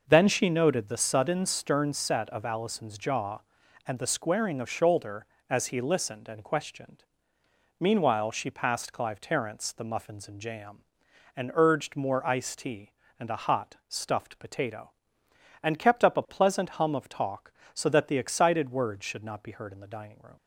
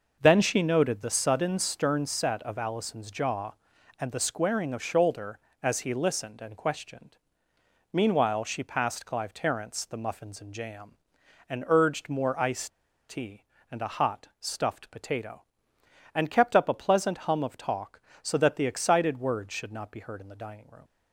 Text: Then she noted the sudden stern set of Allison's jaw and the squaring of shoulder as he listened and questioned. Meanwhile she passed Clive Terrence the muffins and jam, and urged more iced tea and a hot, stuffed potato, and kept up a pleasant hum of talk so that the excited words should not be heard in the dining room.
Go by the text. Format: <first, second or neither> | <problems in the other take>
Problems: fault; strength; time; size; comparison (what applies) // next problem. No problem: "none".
first | pauses between "iced" and "tea"; at 12.6 s; 0.40 s long